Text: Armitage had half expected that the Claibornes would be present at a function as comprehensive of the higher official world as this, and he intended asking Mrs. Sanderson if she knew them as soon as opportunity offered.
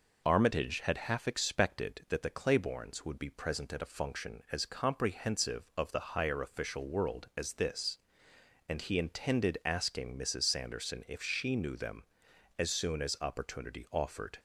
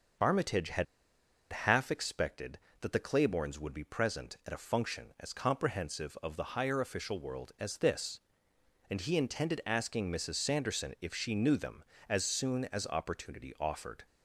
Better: first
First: none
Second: starts louder than the rest; until 1.8 s; 6 dB // pauses between "had" and "half"; noticeable; at 0.8 s; 0.68 s long

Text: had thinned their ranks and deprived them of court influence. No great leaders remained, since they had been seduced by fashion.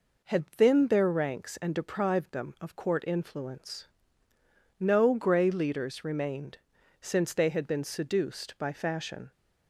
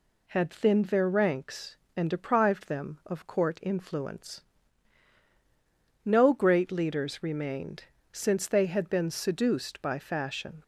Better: second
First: says "grey" for "great"; at 5.1 s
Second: none

